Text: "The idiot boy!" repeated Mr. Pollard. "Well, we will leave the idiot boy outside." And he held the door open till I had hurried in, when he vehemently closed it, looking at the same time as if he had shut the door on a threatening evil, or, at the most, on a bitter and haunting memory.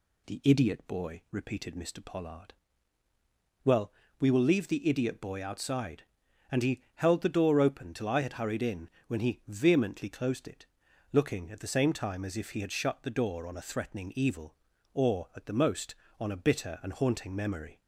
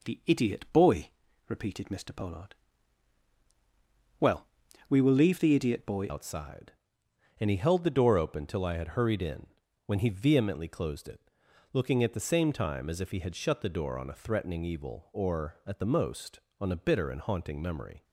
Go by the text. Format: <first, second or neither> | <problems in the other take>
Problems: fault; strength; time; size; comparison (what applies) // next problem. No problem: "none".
first | changes voice at "outside"; from 6.0 s on; 12.0 s long